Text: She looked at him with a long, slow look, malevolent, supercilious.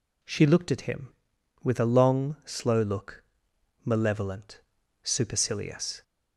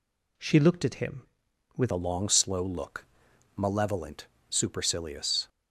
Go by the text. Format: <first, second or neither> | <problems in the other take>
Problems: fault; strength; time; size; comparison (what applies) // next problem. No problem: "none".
first | changes voice at "a"; from 1.9 s on; 3.5 s long